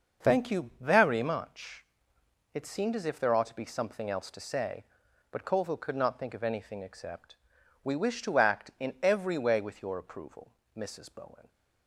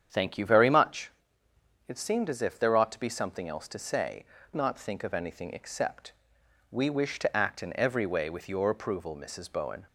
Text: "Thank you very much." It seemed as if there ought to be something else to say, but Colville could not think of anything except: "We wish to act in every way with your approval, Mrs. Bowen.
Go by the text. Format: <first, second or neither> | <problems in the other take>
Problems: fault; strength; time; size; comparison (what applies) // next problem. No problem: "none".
first | starts louder than the rest; strong; until 1.8 s; 8.5 dB; noticeable in the first // skips "but Colville could"; at 4.4 s